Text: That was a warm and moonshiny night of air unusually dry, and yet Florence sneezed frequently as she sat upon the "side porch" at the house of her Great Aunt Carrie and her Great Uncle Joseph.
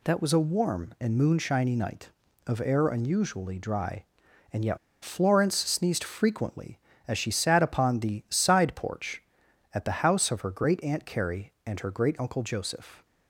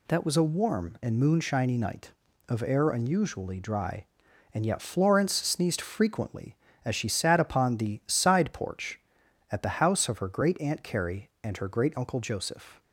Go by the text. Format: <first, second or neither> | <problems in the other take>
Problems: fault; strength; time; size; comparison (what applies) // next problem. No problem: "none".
second | pauses between "yet" and "Florence"; slight; at 4.7 s; 0.25 s long